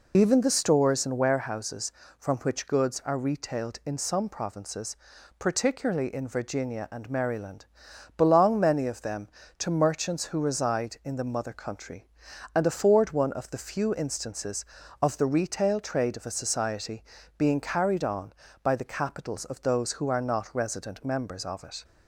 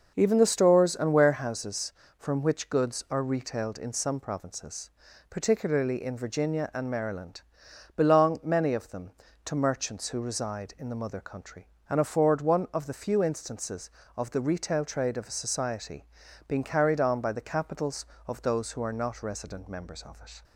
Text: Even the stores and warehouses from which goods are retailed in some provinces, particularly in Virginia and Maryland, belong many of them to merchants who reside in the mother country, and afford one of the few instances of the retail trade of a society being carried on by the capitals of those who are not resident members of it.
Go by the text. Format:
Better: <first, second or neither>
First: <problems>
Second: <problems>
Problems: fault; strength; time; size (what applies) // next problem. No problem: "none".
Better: second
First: loses the start of "Even"; at 0.1 s; 30 ms // pauses between "society" and "being"; slight; at 17.0 s; 0.34 s long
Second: pauses between "society" and "being"; at 16.0 s; 0.42 s long